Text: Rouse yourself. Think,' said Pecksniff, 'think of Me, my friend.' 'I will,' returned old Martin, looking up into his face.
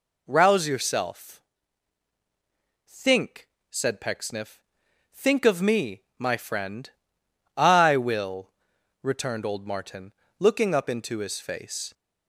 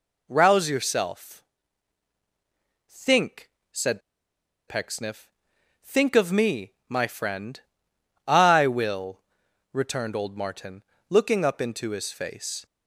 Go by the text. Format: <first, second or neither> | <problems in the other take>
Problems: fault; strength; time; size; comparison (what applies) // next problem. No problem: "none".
first | pauses between "said" and "Pecksniff"; noticeable; at 4.0 s; 0.68 s long